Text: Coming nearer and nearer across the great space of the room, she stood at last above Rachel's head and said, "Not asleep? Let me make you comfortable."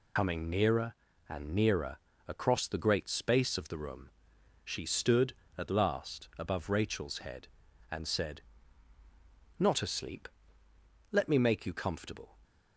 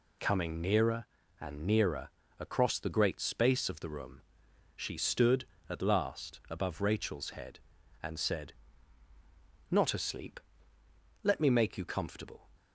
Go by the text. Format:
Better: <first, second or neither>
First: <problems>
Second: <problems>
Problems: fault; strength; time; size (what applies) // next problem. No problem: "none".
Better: second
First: loses the start of "Coming"; at 0.1 s; 75 ms // pauses between "nearer" and "across"; slight; at 1.9 s; 0.30 s long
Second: pauses between "nearer" and "across"; slight; at 2.0 s; 0.30 s long